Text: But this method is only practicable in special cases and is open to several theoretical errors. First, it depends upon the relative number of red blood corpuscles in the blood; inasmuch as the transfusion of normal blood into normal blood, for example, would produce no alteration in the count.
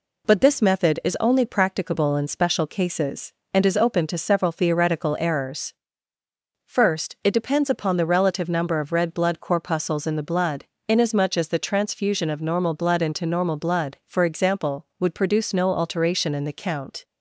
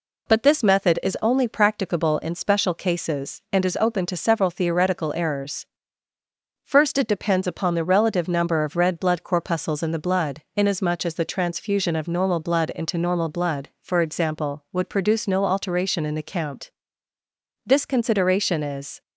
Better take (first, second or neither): first